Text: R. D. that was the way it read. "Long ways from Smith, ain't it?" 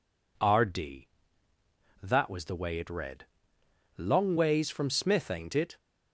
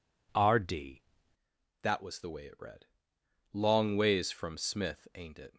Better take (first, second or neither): first